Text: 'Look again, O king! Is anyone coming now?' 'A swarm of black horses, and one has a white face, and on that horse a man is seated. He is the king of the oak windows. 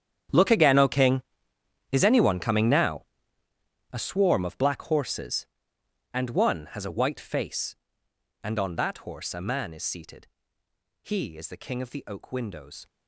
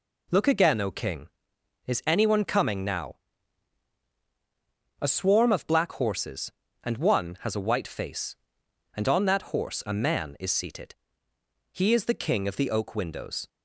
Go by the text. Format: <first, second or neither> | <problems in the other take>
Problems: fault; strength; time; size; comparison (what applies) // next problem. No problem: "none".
second | gets quieter; strong; throughout; 17.5 dB